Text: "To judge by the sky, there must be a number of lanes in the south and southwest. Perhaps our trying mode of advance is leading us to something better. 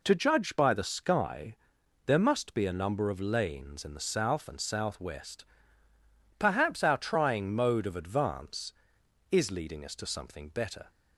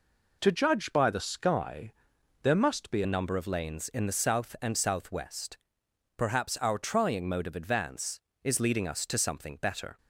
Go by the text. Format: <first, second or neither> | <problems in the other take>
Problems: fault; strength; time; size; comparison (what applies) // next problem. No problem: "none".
first | changes voice at "a"; from 3.0 s on; 6.9 s long